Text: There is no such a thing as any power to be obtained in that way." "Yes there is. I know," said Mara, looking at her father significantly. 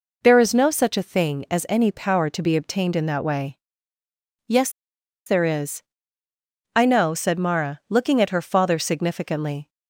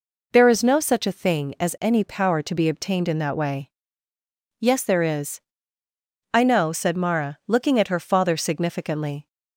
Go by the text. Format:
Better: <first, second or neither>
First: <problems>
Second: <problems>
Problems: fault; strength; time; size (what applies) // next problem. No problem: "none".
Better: second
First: pauses between "Yes" and "there"; noticeable; at 4.6 s; 0.57 s long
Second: none